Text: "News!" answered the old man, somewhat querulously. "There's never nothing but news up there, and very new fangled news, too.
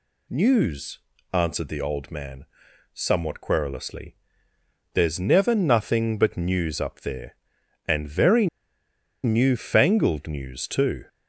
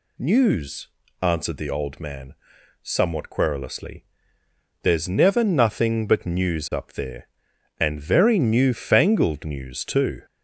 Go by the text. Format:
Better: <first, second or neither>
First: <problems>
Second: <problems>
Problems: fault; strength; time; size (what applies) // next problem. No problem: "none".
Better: second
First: pauses between "very" and "new"; noticeable; at 8.4 s; 0.77 s long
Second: none